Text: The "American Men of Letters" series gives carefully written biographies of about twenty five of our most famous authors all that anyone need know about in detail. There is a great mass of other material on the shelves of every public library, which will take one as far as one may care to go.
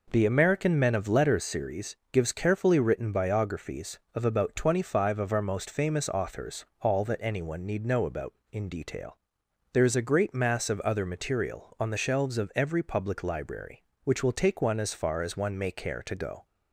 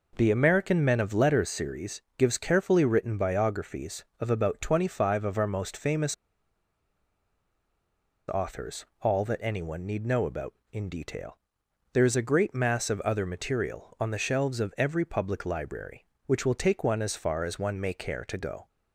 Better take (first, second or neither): first